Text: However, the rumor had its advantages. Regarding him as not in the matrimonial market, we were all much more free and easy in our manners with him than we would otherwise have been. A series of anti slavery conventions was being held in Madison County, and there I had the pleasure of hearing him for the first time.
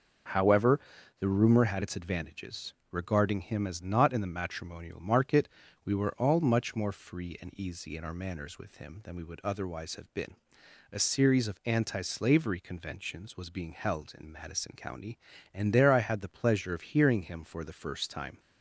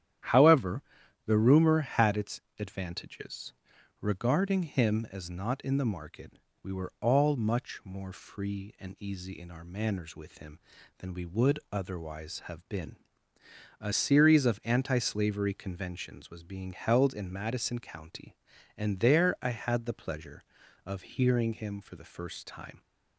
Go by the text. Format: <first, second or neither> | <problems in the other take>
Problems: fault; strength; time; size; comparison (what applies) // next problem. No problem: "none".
first | starts louder than the rest; strong; until 1.7 s; 11 dB // pauses between "its" and "advantages"; slight; at 2.3 s; 0.18 s long // skips "matrimonial"; at 5.8 s